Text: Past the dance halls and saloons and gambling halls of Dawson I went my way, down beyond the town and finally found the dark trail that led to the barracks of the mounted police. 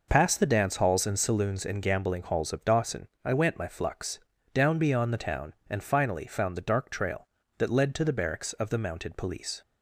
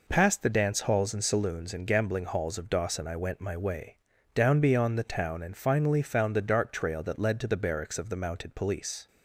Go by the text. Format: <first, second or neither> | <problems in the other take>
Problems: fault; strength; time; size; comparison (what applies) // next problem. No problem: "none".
second | pauses between "Dawson" and "I"; slight; at 3.0 s; 0.16 s long // says "flux" for "way"; at 3.6 s